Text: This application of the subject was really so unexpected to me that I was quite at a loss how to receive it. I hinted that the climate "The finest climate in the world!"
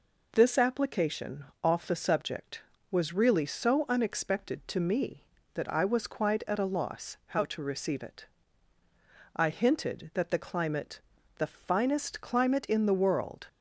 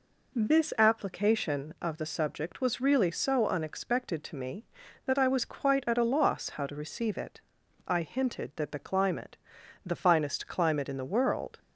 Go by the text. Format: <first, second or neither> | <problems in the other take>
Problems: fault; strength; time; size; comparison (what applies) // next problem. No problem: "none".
second | says "off" for "of"; at 1.6 s // pauses between "climate" and "The"; at 10.9 s; 0.38 s long; noticeable in the second